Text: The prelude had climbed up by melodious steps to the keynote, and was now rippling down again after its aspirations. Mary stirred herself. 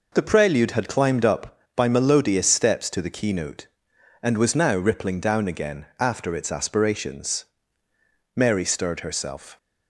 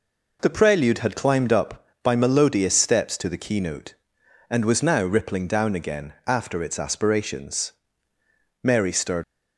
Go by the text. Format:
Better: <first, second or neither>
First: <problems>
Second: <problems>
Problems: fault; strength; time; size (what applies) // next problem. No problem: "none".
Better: first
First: none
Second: stops before "herself"; at 9.2 s